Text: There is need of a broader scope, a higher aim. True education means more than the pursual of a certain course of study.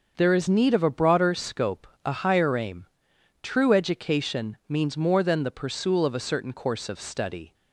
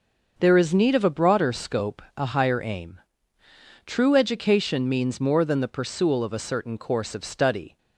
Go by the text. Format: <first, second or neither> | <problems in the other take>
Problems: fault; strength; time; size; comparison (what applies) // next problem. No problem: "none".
neither | starts louder than the rest; the same in both